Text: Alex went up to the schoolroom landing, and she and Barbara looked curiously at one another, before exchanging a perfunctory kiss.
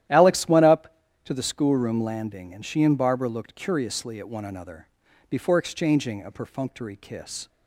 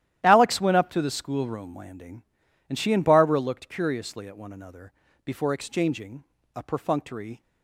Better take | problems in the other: first | starts louder than the rest; strong; until 1.2 s; 12.5 dB; strong in the first // pauses between "exchanging" and "a"; slight; at 6.2 s; 0.30 s long // stops before "kiss"; at 7.4 s

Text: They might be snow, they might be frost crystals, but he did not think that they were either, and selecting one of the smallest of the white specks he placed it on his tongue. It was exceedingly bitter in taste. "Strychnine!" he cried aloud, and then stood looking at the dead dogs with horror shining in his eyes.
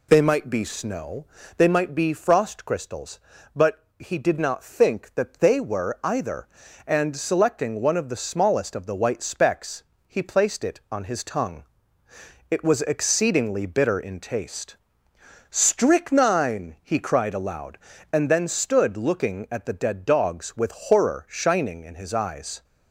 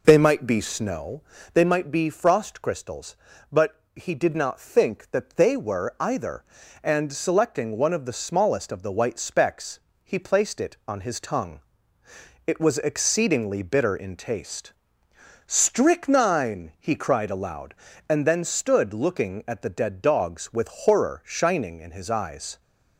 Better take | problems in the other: first | starts louder than the rest; noticeable; until 1.1 s; 5 dB // pauses between "specks" and "he"; slight; at 9.7 s; 0.24 s long; slight in the first

